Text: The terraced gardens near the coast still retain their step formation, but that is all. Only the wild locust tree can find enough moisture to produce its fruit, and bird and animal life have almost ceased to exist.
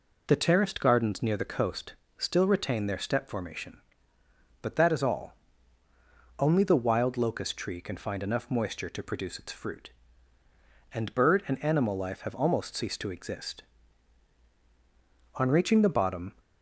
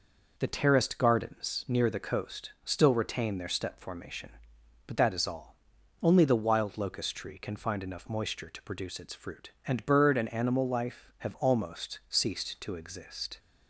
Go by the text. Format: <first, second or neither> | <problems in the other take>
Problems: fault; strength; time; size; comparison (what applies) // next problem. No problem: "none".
second | pauses between "coast" and "still"; slight; at 1.9 s; 0.22 s long // goes on to say "On reaching the bottom"; noticeable; from 15.3 s on; 0.98 s long